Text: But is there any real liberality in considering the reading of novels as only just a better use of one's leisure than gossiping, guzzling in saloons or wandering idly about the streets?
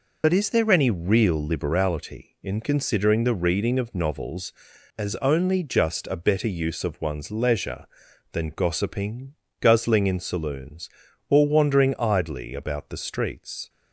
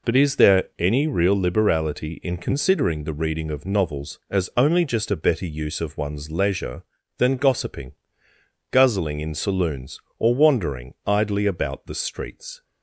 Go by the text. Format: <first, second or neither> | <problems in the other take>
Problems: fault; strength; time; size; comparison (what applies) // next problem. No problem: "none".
second | loses the start of "But"; at 0.2 s; 50 ms